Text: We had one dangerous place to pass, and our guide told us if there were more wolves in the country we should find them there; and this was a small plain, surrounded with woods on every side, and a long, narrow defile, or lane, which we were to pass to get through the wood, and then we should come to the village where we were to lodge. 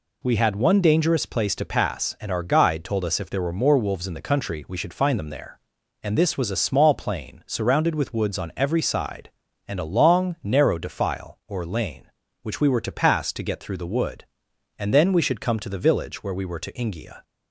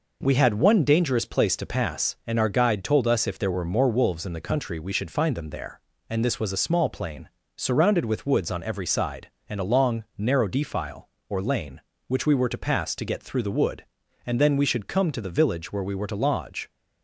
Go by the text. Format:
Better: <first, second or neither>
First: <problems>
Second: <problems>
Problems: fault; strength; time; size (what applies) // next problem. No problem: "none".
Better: second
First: says "ingia" for "lodge"; at 16.7 s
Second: none